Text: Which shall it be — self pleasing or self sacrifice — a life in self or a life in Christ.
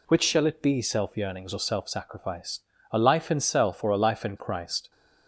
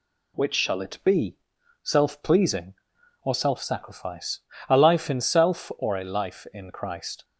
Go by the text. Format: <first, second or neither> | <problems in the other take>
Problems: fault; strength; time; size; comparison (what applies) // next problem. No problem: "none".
second | says "yearnings" for "pleasing"; at 1.1 s